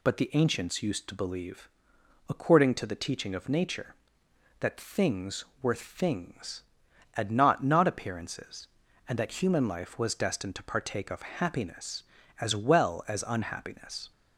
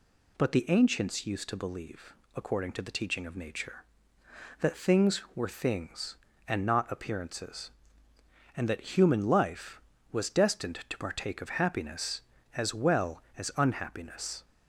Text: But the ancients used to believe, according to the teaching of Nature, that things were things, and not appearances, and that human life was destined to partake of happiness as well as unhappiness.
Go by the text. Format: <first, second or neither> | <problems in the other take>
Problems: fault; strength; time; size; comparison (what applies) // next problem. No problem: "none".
second | says "not" twice; at 7.6 s